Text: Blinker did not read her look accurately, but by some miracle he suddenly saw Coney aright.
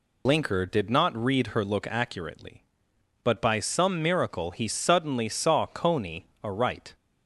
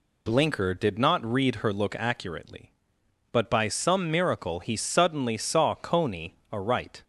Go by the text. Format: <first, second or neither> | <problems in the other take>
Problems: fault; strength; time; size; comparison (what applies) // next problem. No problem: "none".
second | loses the start of "Blinker"; at 0.2 s; 75 ms // pauses between "Coney" and "aright"; slight; at 6.2 s; 0.18 s long; slight in the second